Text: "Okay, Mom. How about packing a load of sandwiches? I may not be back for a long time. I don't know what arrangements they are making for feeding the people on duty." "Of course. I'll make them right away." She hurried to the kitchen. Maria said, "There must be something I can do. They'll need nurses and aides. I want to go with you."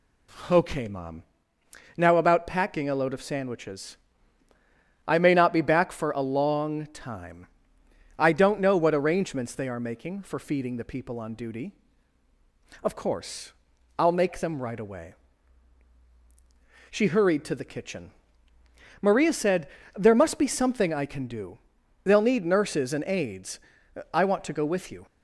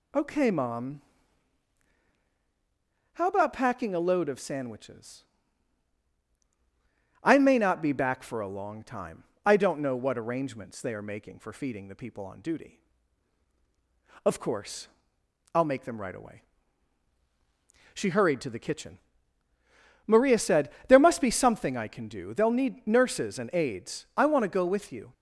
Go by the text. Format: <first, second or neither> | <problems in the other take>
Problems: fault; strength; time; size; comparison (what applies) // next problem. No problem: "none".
second | says "Now" for "How"; at 1.9 s